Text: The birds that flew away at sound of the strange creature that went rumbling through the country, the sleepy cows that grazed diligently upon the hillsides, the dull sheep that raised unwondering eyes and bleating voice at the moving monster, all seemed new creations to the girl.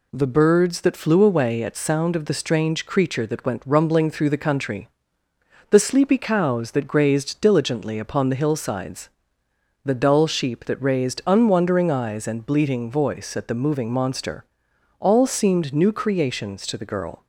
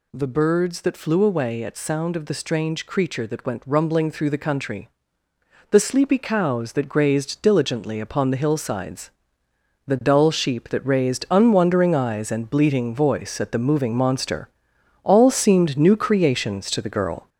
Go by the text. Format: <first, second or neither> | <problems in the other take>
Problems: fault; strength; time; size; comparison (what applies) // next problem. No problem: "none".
first | gets louder; noticeable; throughout; 4.5 dB